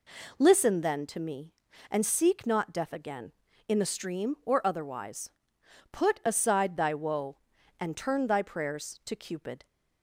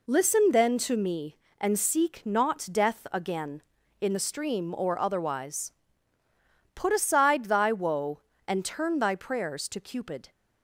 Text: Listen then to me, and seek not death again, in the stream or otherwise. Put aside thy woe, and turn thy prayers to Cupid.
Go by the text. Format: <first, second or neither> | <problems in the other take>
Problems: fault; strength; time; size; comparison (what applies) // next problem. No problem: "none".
neither | none